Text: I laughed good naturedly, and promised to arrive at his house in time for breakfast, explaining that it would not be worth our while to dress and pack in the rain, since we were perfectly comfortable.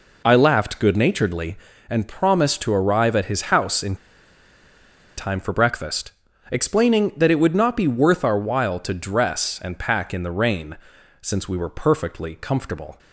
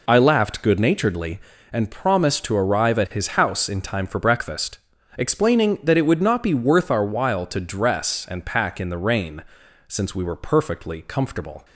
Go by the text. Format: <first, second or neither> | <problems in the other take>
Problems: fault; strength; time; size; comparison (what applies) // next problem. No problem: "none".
second | pauses between "in" and "time"; at 3.9 s; 1.2 s long